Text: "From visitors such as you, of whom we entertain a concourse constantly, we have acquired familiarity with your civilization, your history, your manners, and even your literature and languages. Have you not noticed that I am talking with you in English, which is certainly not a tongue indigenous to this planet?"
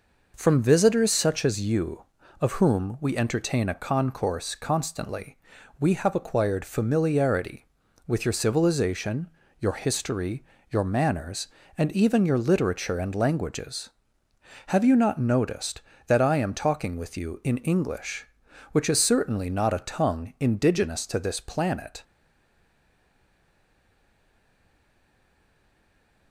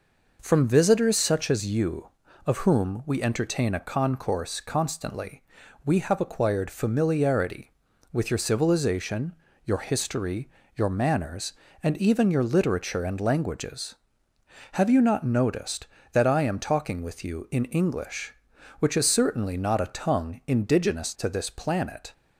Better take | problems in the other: second | stays silent after the last word; strong; from 22.0 s on; 4.3 s long

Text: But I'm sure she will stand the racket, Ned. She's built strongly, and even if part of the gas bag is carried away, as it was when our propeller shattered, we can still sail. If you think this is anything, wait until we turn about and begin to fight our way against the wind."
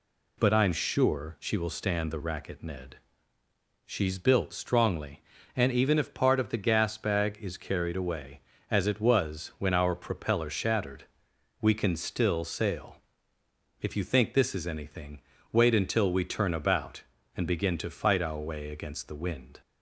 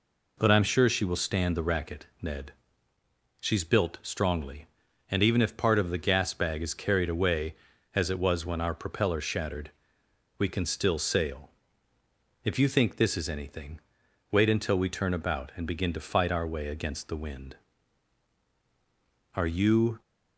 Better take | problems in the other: first | goes on to say "Are you"; noticeable; from 19.3 s on; 0.68 s long

